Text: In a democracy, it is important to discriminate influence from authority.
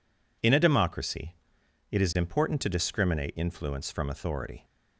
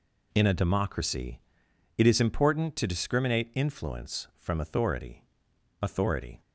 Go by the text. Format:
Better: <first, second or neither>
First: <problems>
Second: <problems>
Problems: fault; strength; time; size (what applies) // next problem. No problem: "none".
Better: first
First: none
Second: says "authority" twice; at 5.8 s